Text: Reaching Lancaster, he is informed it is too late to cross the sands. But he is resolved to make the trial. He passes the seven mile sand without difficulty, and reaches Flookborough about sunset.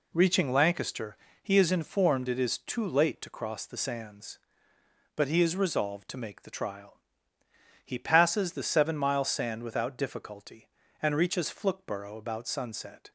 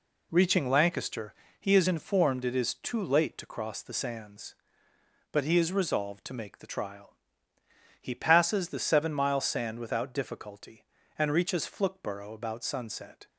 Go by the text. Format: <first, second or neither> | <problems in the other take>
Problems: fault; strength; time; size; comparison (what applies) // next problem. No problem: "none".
neither | none